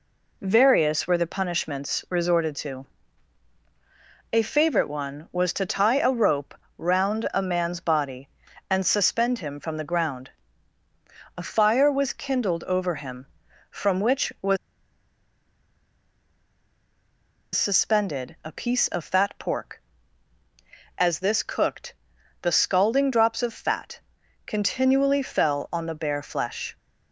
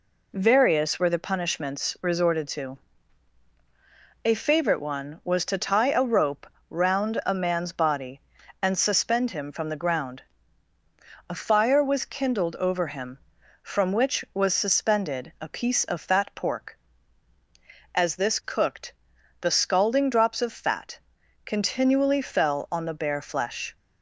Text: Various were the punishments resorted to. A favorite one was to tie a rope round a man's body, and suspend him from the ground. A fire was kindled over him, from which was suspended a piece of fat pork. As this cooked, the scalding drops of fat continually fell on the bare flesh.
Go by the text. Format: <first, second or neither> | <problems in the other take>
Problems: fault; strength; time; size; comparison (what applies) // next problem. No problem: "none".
second | pauses between "rope" and "round"; slight; at 6.5 s; 0.22 s long; slight in the second // pauses between "was" and "suspended"; strong; at 14.5 s; 2.9 s long // pauses between "fat" and "continually"; noticeable; at 23.9 s; 0.46 s long; noticeable in the second